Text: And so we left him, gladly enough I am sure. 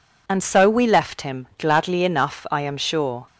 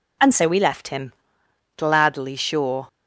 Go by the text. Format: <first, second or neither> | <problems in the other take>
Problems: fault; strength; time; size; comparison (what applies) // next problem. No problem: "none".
first | skips "enough I am"; at 2.3 s